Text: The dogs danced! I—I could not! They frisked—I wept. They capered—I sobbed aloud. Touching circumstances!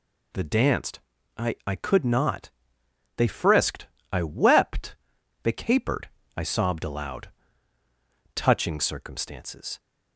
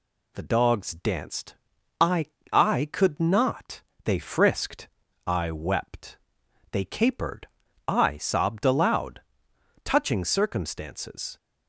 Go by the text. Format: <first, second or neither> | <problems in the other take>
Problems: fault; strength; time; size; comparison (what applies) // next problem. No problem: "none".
second | skips "dogs"; at 0.4 s